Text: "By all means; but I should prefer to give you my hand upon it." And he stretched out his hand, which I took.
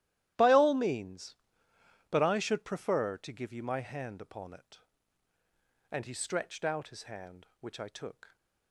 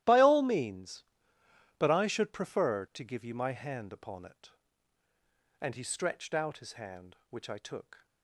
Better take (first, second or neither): neither